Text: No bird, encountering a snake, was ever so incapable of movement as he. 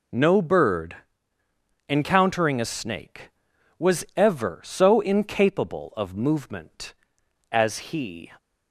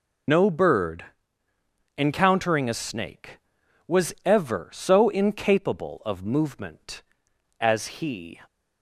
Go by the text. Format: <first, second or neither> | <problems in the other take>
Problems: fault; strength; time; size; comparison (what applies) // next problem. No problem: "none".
first | loses the start of "No"; at 0.2 s; 70 ms